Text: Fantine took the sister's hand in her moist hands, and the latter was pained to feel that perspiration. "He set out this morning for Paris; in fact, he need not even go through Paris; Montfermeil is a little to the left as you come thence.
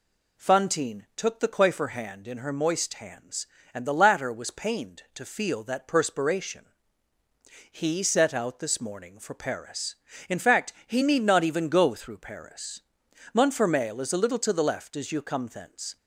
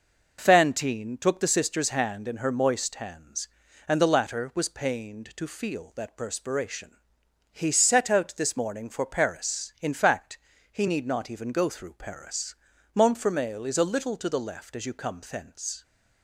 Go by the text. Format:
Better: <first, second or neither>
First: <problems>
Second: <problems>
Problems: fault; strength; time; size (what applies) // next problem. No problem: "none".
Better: second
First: says "coiffer" for "sister's"; at 1.4 s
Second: none